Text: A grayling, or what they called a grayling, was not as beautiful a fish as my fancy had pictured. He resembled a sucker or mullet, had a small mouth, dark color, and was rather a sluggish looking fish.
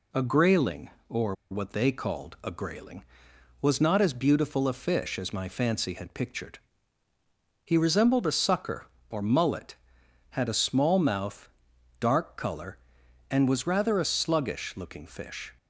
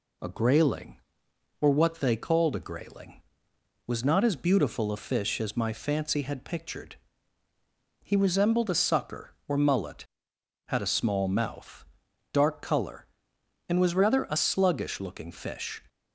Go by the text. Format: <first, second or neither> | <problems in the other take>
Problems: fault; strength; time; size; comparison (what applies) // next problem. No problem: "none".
second | pauses between "or" and "what"; slight; at 1.3 s; 0.17 s long